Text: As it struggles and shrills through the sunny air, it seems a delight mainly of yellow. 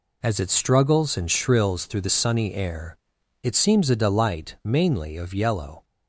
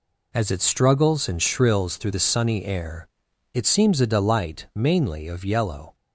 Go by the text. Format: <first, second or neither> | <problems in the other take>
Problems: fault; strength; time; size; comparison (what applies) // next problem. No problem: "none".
neither | none